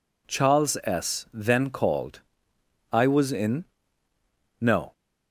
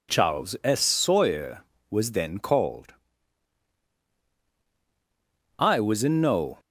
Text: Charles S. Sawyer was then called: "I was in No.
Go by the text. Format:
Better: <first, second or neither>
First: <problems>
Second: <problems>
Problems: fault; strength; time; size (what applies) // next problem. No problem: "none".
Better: second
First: skips "Sawyer was"; at 1.2 s // pauses between "in" and "No"; noticeable; at 3.6 s; 0.96 s long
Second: none